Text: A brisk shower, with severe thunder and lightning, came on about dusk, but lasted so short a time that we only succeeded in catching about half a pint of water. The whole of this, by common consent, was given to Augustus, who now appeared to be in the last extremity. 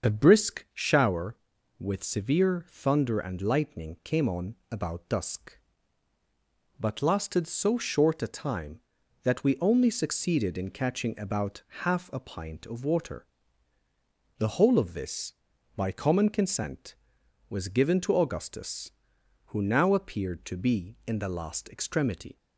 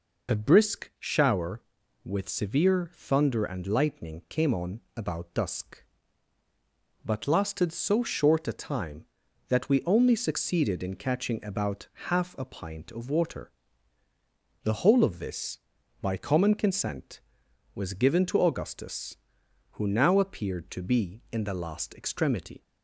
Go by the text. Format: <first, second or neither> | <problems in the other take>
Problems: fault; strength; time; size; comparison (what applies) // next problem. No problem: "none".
second | starts louder than the rest; until 1.2 s; 6.5 dB // pauses between "on" and "about"; slight; at 4.5 s; 0.16 s long; slight in the second // pauses between "about" and "half"; slight; at 11.6 s; 0.22 s long; slight in the second